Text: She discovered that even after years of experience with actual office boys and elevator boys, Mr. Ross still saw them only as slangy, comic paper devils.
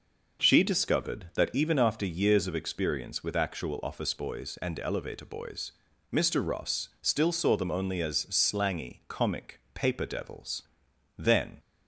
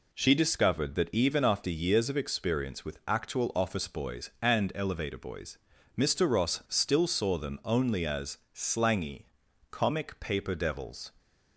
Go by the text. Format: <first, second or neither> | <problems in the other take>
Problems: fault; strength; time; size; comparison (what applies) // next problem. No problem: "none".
second | pauses between "comic" and "paper"; slight; at 9.5 s; 0.16 s long // goes on to say "Then"; slight; from 11.1 s on; 0.42 s long